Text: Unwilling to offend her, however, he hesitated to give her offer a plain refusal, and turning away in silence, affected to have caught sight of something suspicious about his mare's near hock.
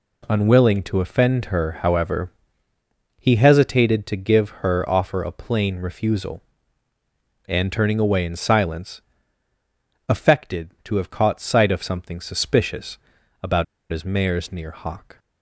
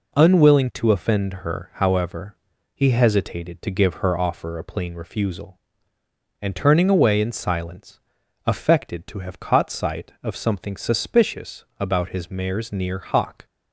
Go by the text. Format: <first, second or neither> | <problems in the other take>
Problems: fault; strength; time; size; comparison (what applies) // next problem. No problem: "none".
second | pauses between "suspicious" and "about"; at 12.9 s; 0.44 s long; slight in the second // pauses between "about" and "his"; slight; at 13.6 s; 0.25 s long